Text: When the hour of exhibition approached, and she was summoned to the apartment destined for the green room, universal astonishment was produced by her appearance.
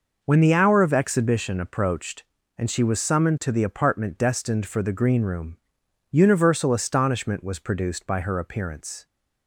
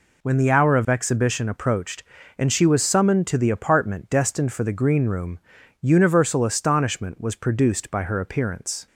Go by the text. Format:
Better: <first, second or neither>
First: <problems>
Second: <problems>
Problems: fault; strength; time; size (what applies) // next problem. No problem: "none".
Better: neither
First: none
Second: none